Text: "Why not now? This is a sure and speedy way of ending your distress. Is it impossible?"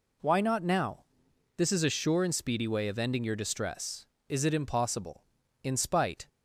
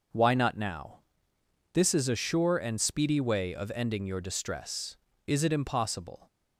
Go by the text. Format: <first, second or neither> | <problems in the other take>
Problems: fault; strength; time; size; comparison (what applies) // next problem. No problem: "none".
second | goes on to say "In spite"; noticeable; from 5.6 s on; 0.64 s long